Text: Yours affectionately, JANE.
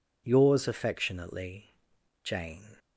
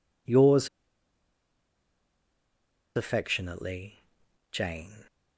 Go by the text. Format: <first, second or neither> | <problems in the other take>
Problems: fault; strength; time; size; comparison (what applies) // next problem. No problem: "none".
first | pauses between "Yours" and "affectionately"; strong; at 0.6 s; 2.2 s long